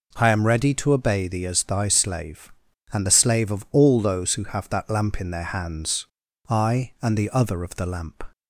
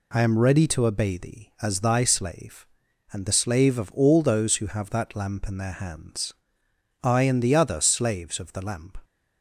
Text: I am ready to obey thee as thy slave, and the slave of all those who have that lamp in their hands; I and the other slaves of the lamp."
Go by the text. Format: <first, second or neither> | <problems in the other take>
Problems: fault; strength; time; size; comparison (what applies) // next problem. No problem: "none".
second | skips "slaves"; at 7.6 s